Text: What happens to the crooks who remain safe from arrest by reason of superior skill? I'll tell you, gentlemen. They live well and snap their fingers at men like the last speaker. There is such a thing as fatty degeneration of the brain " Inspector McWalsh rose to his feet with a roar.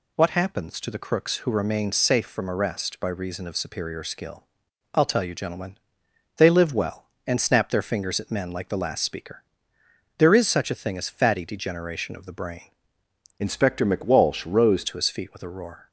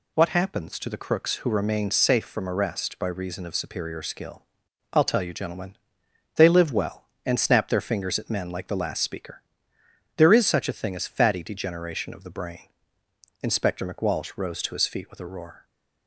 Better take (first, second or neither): second